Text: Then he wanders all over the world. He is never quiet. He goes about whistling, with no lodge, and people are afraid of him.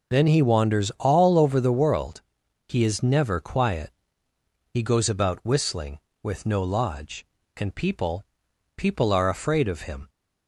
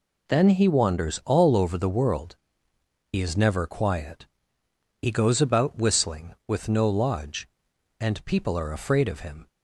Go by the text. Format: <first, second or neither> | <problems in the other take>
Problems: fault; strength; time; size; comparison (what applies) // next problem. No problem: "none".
second | says "people" twice; at 8.7 s